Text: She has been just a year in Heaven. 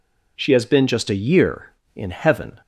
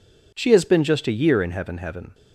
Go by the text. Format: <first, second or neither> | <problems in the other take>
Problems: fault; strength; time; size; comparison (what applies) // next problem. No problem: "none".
first | says "Heaven" twice; at 1.7 s